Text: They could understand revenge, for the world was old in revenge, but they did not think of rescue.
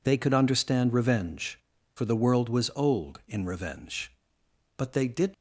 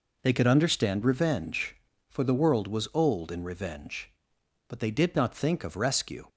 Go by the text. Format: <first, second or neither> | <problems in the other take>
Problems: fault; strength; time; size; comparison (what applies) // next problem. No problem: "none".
second | stops before "not think of rescue"; at 5.3 s